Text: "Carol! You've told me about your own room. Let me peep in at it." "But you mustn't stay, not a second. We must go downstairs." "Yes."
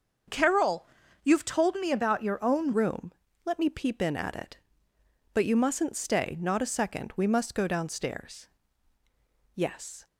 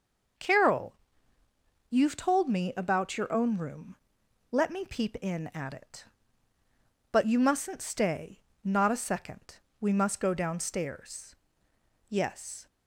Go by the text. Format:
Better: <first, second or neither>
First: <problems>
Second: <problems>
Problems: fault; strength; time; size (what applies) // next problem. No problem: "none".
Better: second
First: starts louder than the rest; until 1.6 s; 6.5 dB // changes voice at "room"; from 2.7 s on; 7.3 s long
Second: none